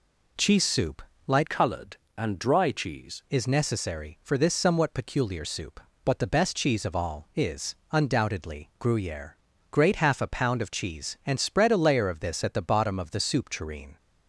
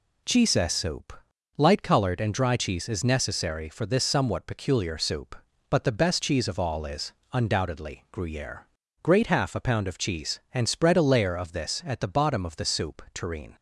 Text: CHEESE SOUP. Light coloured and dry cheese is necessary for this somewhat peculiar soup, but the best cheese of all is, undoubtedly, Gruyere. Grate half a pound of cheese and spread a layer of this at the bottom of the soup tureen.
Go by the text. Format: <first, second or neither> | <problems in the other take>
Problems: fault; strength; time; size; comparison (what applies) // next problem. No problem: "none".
second | changes voice from "coloured" to "cheese"; from 1.4 to 3.2 s; 1.8 s long